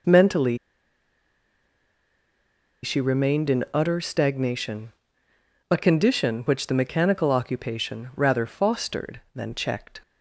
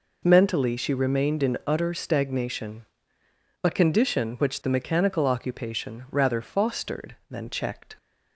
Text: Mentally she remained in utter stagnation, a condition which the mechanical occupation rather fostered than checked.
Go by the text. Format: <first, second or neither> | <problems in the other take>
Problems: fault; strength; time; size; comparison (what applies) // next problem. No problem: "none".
second | pauses between "Mentally" and "she"; strong; at 0.5 s; 2.2 s long